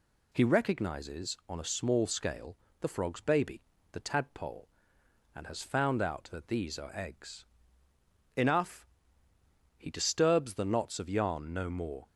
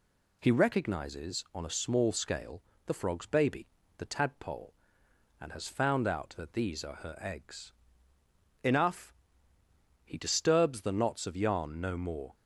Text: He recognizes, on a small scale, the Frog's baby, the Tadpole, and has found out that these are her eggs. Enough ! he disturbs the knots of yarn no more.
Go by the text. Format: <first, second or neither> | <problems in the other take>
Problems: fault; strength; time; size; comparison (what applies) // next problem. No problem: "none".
second | skips "her"; at 6.9 s